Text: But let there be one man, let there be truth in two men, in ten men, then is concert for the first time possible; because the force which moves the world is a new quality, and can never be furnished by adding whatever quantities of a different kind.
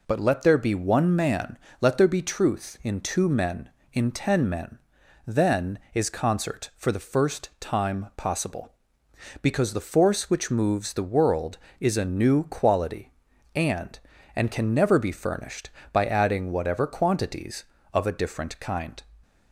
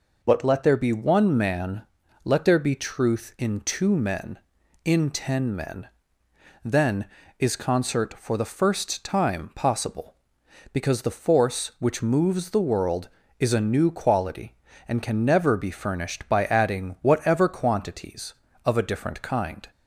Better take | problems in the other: second | says "and" twice; at 14.3 s

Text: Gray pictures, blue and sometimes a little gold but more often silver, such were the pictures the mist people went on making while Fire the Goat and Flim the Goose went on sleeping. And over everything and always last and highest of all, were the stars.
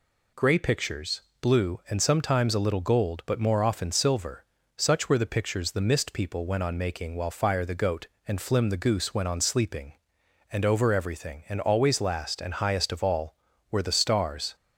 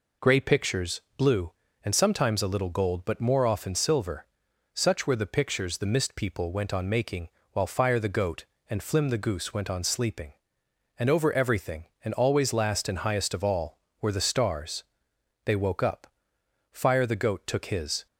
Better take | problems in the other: first | pauses between "making" and "while"; slight; at 7.2 s; 0.24 s long // goes on to say "They woke up Fire the Goat took his"; strong; from 15.4 s on; 2.6 s long

